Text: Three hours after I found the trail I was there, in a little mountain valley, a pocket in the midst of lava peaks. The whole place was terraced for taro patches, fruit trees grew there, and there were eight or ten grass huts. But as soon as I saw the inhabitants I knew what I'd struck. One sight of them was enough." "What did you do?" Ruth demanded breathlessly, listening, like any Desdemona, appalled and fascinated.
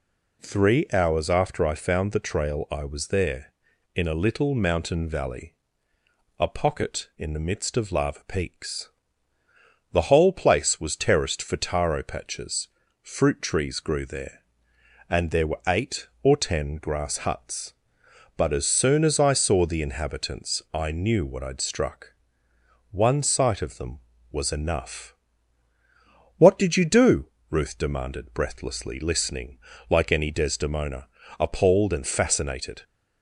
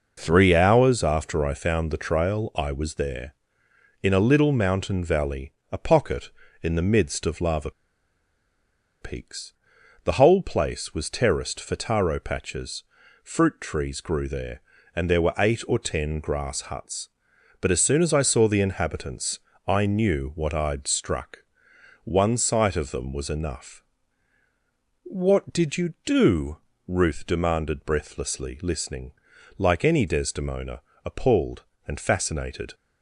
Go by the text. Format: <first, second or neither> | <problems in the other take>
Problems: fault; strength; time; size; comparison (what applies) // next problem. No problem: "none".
first | pauses between "lava" and "peaks"; strong; at 7.7 s; 1.3 s long // pauses between "inhabitants" and "I"; slight; at 19.3 s; 0.30 s long